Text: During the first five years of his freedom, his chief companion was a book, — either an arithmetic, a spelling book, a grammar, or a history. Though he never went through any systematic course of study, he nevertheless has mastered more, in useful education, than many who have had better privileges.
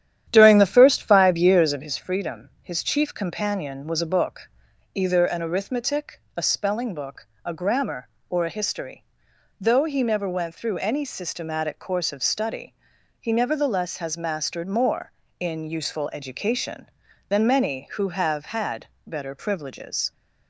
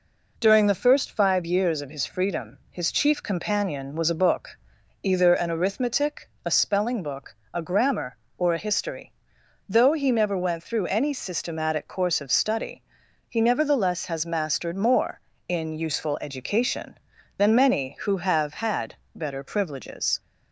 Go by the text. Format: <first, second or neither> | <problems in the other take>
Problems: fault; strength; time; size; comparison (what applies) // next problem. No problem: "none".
second | starts louder than the rest; strong; until 1.9 s; 10.5 dB // pauses between "had" and "better"; slight; at 18.8 s; 0.20 s long; slight in the second